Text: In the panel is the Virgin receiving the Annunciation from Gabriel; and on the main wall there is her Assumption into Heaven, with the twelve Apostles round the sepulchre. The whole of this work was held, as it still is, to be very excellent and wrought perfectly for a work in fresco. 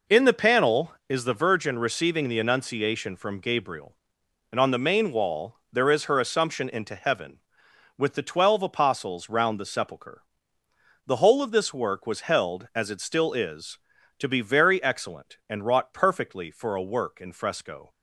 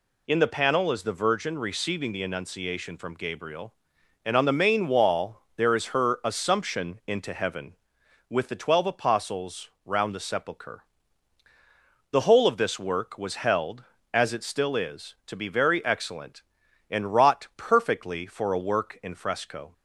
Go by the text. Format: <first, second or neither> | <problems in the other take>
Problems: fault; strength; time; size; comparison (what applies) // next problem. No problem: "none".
neither | pauses between "wall" and "there"; slight; the same in both